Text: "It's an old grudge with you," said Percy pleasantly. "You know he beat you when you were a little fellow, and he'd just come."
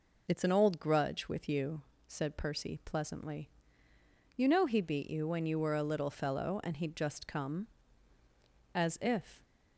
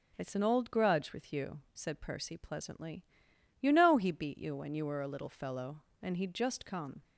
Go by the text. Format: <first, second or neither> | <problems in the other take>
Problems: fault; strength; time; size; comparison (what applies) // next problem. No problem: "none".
second | goes on to say "As if"; noticeable; from 8.7 s on; 0.70 s long